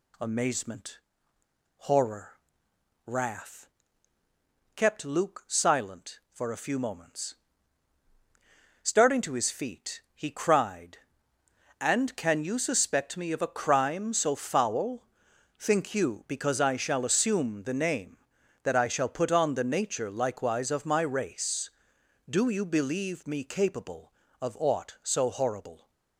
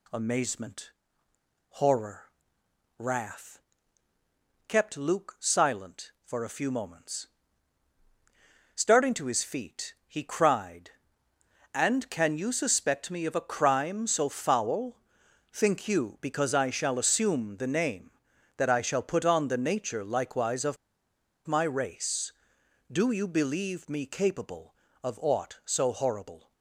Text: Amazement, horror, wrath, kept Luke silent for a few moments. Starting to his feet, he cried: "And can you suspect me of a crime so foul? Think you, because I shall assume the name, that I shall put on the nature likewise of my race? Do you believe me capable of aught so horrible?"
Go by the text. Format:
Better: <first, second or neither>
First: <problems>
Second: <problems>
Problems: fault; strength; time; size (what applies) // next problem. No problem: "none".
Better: first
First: none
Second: pauses between "of" and "my"; noticeable; at 20.7 s; 0.71 s long